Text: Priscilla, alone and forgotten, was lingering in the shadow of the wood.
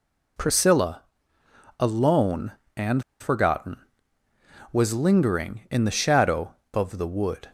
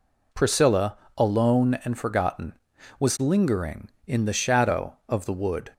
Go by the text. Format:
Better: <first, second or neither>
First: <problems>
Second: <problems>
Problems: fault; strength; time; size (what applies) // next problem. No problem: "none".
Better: second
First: pauses between "and" and "forgotten"; slight; at 3.0 s; 0.17 s long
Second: none